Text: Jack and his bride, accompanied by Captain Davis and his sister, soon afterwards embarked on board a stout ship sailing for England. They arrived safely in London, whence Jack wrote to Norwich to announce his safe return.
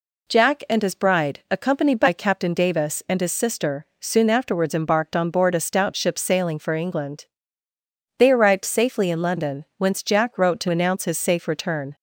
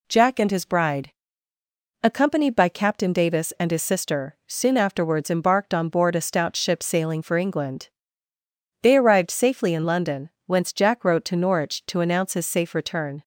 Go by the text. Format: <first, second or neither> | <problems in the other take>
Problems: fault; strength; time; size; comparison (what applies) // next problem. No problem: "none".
second | skips "Norwich to"; at 10.6 s